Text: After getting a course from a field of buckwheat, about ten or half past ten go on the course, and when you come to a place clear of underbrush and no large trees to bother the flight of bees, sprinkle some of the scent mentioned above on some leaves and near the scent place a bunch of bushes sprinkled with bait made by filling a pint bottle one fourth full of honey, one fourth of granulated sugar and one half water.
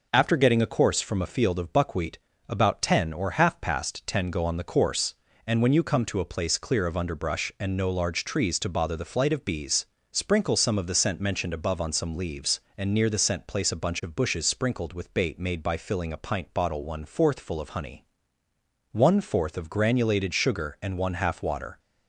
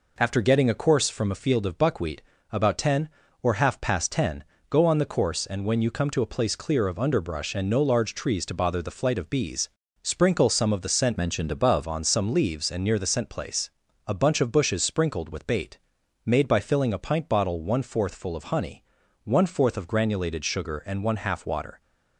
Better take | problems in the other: first | pauses between "ten" and "go"; slight; at 4.4 s; 0.26 s long // changes voice from "mentioned" to "above"; from 11.1 to 11.8 s; 0.7 s long // pauses between "place" and "a"; slight; at 13.7 s; 0.36 s long // pauses between "bait" and "made"; noticeable; at 15.7 s; 0.46 s long

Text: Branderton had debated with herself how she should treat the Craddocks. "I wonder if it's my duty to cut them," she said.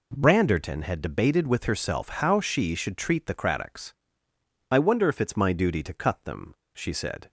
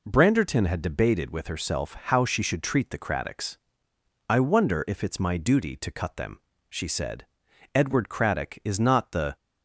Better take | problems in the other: first | goes on to say "Edward Craddock is not the"; from 7.7 s on; 1.6 s long

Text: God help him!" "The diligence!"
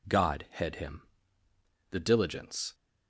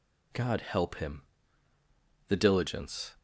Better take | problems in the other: second | says "head" for "help"; at 0.5 s

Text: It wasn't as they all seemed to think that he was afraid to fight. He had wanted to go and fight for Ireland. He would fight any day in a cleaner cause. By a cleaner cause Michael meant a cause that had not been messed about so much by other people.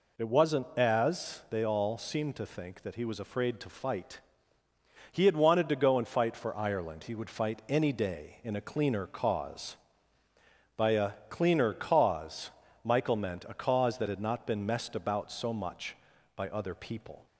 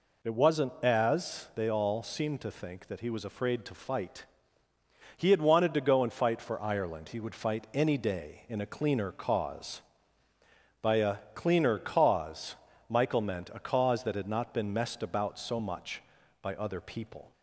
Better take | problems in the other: neither | pauses between "a" and "cleaner"; slight; the same in both // pauses between "cause" and "Michael"; slight; the same in both

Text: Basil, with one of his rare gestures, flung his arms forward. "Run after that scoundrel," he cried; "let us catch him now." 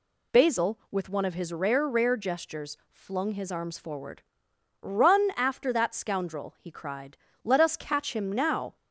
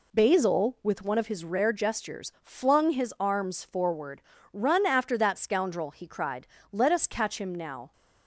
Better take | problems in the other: second | says "rare" twice; at 1.8 s

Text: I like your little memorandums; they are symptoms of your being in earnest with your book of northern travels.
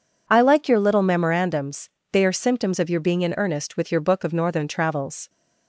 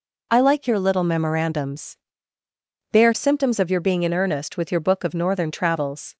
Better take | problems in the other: neither | none

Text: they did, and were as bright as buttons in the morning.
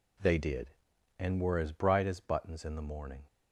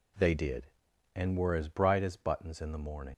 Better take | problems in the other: first | leaves "morning" unfinished; at 3.1 s; 85 ms

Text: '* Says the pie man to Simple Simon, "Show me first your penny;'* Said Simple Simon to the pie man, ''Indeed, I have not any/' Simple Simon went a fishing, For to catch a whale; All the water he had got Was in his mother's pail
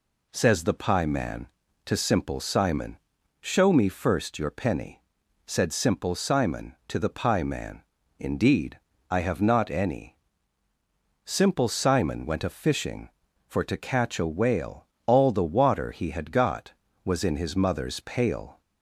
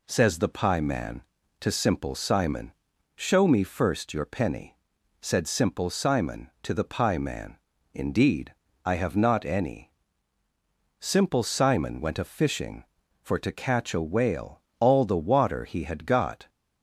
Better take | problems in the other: first | stops before "Was in his mother's pail"; at 16.4 s

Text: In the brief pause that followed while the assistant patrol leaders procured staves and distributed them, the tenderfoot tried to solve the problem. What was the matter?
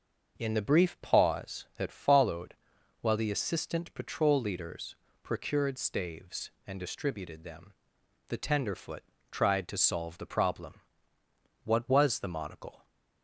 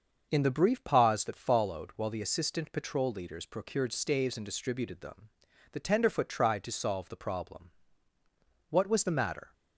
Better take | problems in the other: second | starts louder than the rest; until 1.3 s; 6.5 dB; also in the second // pauses between "followed" and "while"; noticeable; at 2.5 s; 0.48 s long // pauses between "leaders" and "procured"; slight; at 4.9 s; 0.28 s long // pauses between "tenderfoot" and "tried"; slight; at 9.0 s; 0.28 s long // says "monocle" for "matter"; at 12.2 s

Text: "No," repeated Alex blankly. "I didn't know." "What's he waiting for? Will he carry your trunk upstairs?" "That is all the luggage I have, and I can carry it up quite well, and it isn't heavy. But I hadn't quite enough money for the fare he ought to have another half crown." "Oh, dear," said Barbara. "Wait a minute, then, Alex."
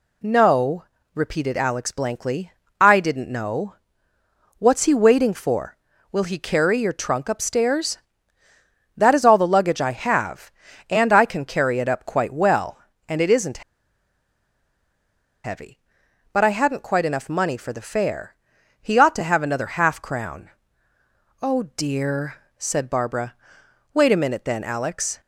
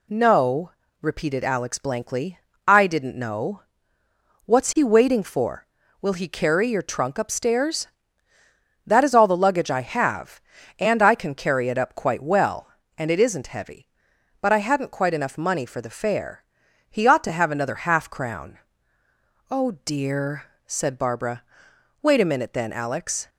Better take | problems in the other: second | pauses between "isn't" and "heavy"; strong; at 13.6 s; 1.8 s long // pauses between "fare" and "he"; noticeable; at 18.3 s; 0.50 s long; noticeable in the second

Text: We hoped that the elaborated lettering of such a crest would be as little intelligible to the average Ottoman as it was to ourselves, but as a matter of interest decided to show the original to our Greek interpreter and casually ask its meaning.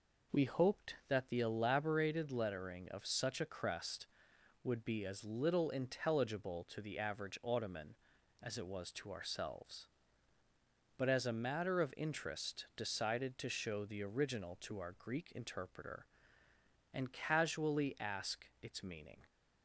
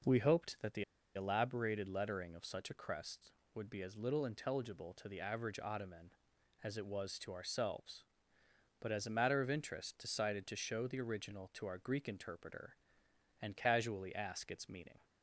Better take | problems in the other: first | pauses between "the" and "elaborated"; slight; at 0.8 s; 0.32 s long

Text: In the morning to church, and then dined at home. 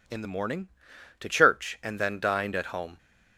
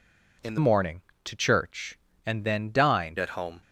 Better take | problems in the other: first | changes voice from "morning" to "dined"; from 0.5 to 3.1 s; 2.6 s long

